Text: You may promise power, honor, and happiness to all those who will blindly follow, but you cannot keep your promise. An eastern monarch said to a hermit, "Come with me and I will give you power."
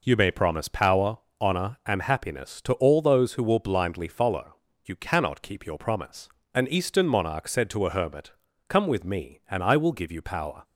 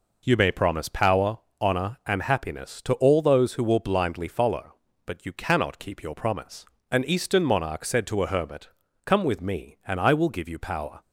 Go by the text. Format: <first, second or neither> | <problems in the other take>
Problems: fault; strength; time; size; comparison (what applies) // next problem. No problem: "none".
second | skips "but"; at 4.7 s